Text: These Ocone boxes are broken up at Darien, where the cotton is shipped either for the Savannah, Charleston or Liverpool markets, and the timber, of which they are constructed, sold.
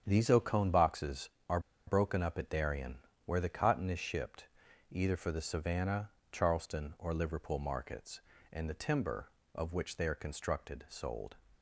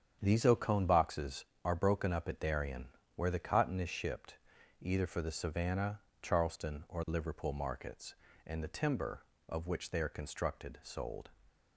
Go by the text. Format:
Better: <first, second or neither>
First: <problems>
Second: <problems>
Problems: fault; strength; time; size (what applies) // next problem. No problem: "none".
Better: second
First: starts louder than the rest; strong; until 1.0 s; 8 dB // pauses between "are" and "broken"; slight; at 1.5 s; 0.27 s long // pauses between "shipped" and "either"; at 4.4 s; 0.42 s long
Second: starts louder than the rest; strong; until 1.2 s; 8 dB // pauses between "shipped" and "either"; at 4.3 s; 0.42 s long